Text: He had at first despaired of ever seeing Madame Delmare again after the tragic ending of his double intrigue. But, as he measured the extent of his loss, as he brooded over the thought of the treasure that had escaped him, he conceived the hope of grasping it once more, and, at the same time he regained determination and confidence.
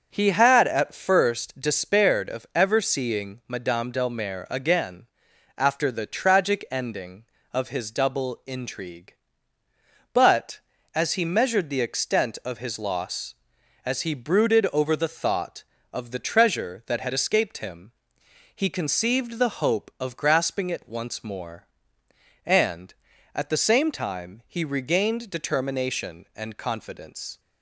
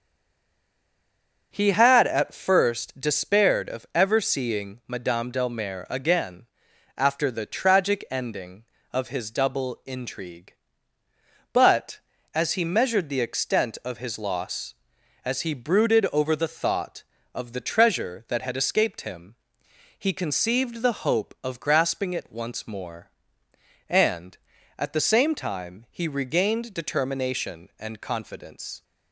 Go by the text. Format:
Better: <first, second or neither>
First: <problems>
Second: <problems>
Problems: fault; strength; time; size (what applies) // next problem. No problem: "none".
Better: first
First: starts louder than the rest; until 1.1 s; 6.5 dB // pauses between "again" and "after"; noticeable; at 5.0 s; 0.52 s long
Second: stays silent before the first word; noticeable; until 1.5 s; 1.5 s long // starts louder than the rest; until 2.5 s; 6.5 dB // pauses between "again" and "after"; noticeable; at 6.4 s; 0.52 s long